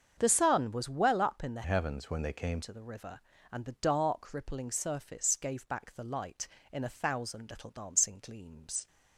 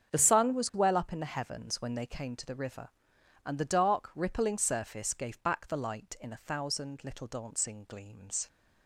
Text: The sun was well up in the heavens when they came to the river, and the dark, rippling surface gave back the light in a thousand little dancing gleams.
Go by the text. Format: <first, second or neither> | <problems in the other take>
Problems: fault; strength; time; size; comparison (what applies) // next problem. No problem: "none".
second | starts louder than the rest; strong; until 1.1 s; 7 dB; strong in the second // changes voice from "heavens" to "came"; from 1.6 to 2.5 s; 0.9 s long